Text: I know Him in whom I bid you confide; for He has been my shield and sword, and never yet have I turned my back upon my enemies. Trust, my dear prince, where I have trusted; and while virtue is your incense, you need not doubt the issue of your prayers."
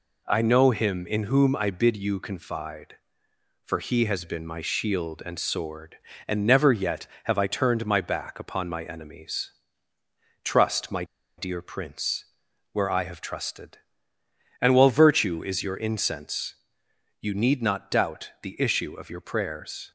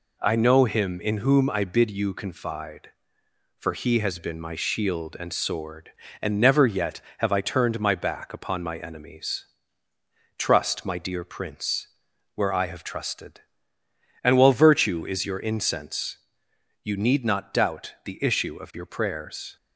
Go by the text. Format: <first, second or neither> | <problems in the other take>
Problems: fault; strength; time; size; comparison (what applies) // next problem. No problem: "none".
second | pauses between "my" and "dear"; slight; at 11.0 s; 0.34 s long